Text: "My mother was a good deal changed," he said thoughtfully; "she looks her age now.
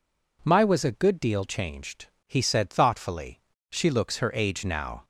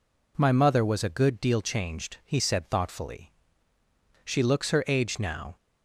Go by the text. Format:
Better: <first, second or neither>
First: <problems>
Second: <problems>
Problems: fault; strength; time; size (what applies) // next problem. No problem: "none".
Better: second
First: skips "mother"; at 0.6 s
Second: none